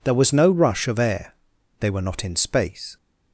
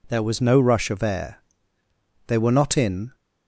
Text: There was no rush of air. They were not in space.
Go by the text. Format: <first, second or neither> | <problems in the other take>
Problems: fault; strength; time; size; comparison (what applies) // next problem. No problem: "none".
first | stops before "space"; at 3.1 s